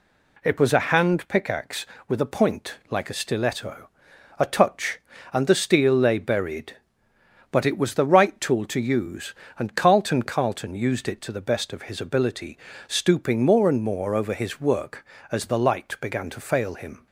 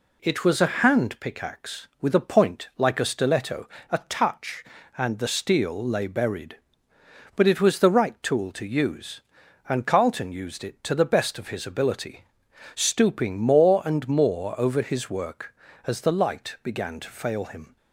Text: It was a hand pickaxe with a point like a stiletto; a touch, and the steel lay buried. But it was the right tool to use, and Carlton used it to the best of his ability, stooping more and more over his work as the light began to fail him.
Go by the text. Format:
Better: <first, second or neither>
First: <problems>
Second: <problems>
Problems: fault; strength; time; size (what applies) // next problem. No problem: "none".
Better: second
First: pauses between "point" and "like"; slight; at 2.7 s; 0.16 s long // says "Carlton" twice; at 10.2 s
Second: none